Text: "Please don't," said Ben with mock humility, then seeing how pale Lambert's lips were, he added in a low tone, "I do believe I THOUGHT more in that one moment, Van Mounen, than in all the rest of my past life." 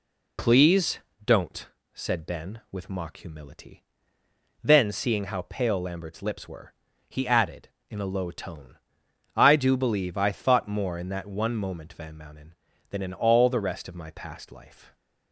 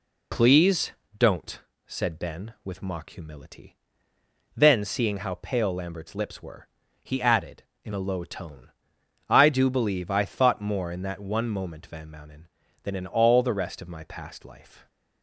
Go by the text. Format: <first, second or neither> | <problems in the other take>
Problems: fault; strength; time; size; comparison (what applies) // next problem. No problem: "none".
neither | pauses between "Please" and "don't"; slight; the same in both